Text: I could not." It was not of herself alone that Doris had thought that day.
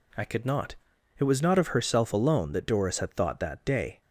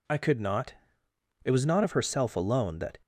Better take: first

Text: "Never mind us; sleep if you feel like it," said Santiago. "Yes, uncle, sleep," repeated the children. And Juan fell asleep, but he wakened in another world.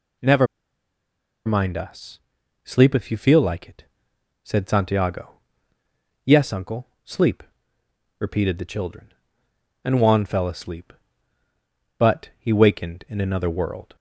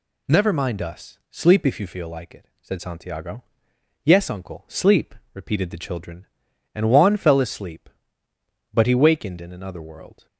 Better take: second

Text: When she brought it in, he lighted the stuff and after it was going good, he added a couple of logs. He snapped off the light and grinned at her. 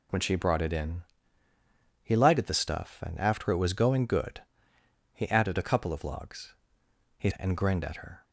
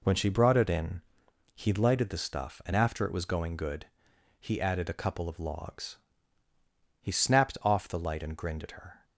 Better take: second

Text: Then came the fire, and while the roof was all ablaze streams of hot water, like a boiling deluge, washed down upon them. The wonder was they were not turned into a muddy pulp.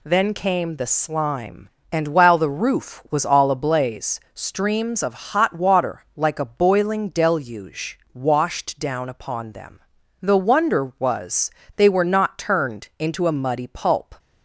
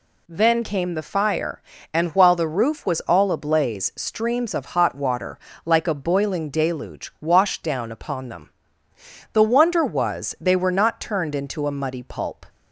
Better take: second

